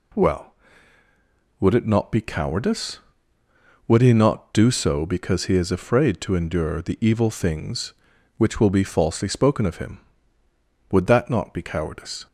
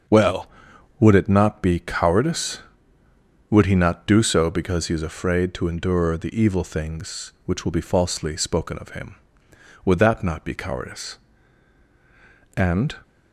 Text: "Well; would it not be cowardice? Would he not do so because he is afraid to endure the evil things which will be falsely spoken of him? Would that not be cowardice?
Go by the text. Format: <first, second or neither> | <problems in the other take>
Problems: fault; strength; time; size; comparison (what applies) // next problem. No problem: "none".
first | starts louder than the rest; until 1.6 s; 6.5 dB // goes on to say "And"; slight; from 12.5 s on; 0.40 s long